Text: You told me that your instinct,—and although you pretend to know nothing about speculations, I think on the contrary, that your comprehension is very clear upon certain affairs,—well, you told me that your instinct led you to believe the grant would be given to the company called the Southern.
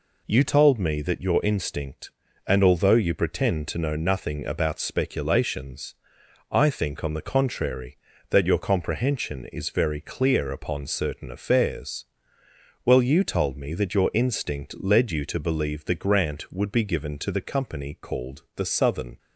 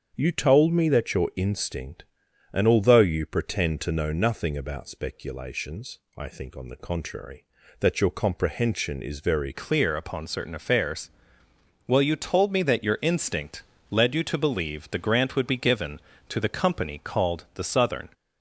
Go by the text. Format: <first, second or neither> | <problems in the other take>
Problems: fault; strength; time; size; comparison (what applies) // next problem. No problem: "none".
first | starts louder than the rest; strong; until 1.1 s; 7.5 dB // changes voice at "clear"; from 9.5 s on; 8.5 s long // pauses between "instinct" and "led"; slight; at 13.6 s; 0.26 s long